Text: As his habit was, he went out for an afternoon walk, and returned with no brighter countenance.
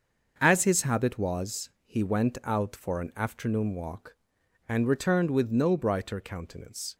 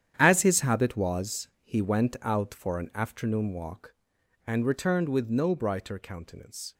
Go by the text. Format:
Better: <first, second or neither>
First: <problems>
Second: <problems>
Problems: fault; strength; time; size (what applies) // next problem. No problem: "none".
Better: first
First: starts louder than the rest; until 1.4 s; 6.5 dB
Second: gets quieter; strong; throughout; 12.5 dB // starts louder than the rest; strong; until 1.1 s; 9.5 dB